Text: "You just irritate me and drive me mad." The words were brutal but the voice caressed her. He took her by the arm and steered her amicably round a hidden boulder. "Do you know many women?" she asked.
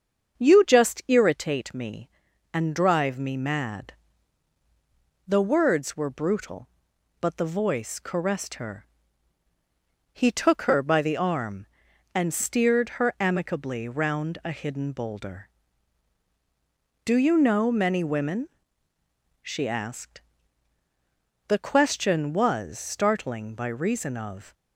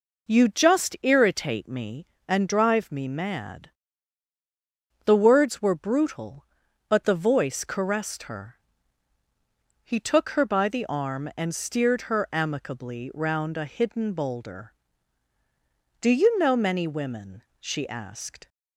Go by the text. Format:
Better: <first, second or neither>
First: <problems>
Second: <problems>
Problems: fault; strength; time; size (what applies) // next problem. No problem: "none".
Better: second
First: starts louder than the rest; until 1.4 s; 7 dB // goes on to say "The question was startling by reason of"; strong; from 21.4 s on; 3.0 s long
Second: none